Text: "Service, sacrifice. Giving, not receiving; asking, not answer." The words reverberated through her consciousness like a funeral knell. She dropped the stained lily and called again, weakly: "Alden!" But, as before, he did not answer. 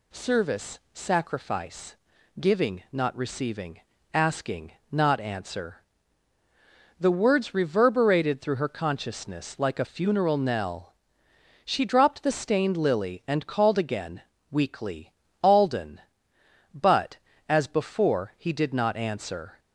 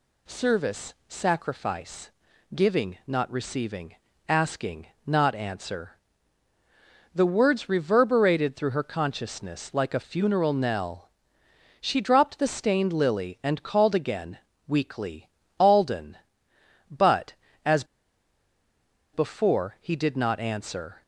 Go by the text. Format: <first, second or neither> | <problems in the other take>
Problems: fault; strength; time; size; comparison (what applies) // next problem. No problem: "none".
first | pauses between "as" and "before"; strong; at 17.8 s; 1.2 s long